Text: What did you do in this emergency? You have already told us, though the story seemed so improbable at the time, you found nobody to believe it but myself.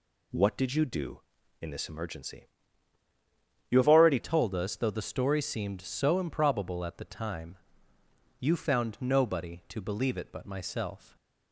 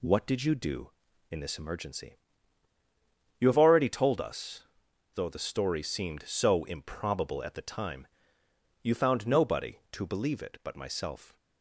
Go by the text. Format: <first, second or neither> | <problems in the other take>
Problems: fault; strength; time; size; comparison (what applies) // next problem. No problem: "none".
second | changes voice at "told"; from 4.1 s on; 7.0 s long